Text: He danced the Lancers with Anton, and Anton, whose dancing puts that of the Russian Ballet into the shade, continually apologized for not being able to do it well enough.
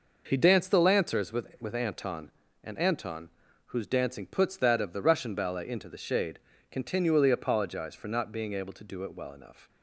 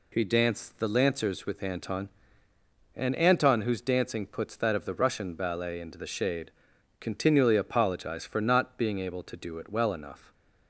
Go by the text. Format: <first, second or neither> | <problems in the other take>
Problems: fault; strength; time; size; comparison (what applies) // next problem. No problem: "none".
second | says "with" twice; at 1.6 s